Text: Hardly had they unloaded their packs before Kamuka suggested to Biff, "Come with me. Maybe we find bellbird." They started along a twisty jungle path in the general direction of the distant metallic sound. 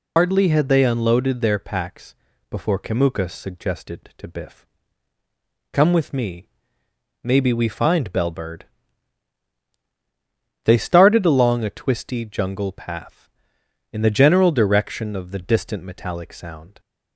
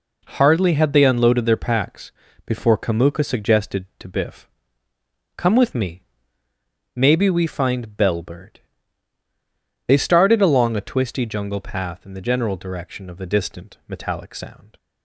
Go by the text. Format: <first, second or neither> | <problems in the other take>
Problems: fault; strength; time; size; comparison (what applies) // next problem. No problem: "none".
second | loses the start of "Hardly"; at 0.1 s; 90 ms // pauses between "packs" and "before"; slight; at 2.1 s; 0.34 s long; slight in the second